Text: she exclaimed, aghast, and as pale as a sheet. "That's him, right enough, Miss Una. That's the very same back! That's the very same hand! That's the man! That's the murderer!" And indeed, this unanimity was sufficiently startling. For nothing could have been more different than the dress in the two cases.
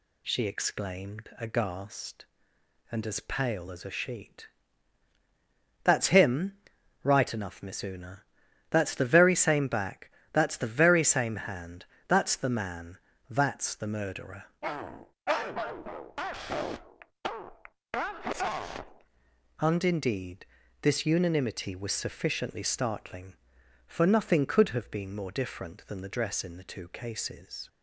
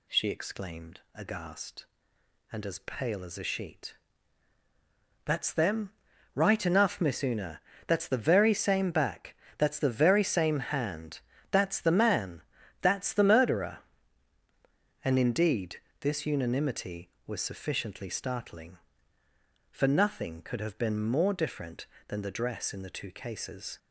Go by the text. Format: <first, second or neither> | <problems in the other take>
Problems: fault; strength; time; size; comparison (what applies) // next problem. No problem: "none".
first | says "them" for "him"; at 5.5 s